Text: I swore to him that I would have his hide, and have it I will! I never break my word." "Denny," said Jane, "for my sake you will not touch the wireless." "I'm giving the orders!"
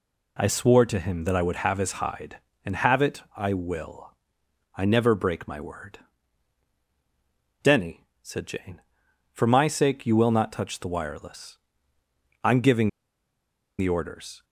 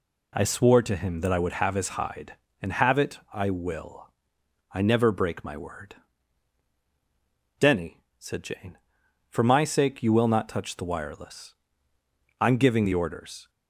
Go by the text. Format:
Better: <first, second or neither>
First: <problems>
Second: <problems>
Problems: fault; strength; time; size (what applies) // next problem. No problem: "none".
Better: second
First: pauses between "giving" and "the"; noticeable; at 12.8 s; 0.89 s long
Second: none